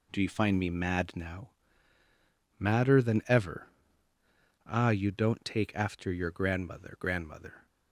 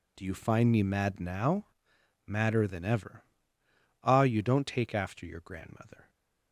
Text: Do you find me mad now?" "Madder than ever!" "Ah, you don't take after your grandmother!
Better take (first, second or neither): second